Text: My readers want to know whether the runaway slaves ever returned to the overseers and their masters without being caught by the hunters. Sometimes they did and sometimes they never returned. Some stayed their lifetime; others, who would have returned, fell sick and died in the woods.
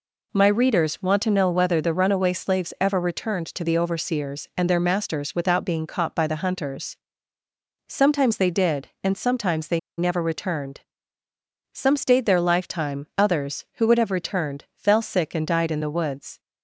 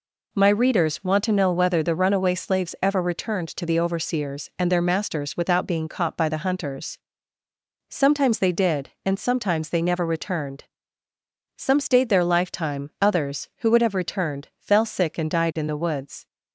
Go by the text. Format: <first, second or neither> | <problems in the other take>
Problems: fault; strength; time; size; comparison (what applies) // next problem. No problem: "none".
second | pauses between "they" and "never"; slight; at 9.7 s; 0.18 s long